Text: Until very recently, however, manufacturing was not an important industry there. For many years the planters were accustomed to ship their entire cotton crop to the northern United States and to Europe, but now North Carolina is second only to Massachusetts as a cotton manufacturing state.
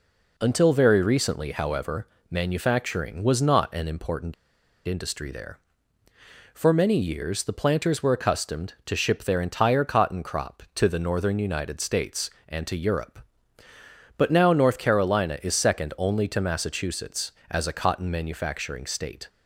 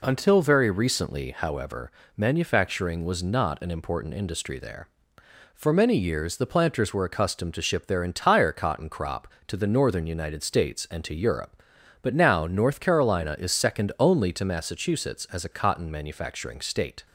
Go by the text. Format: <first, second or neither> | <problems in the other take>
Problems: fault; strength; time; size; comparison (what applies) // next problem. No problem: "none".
second | pauses between "important" and "industry"; noticeable; at 4.3 s; 0.53 s long